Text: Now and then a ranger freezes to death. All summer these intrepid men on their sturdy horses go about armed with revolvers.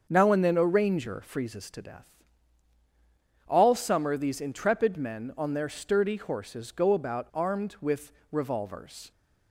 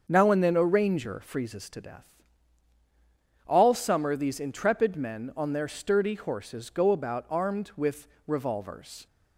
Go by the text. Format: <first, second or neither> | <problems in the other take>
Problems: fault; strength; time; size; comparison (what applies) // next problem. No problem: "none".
neither | starts louder than the rest; the same in both // pauses between "with" and "revolvers"; slight; the same in both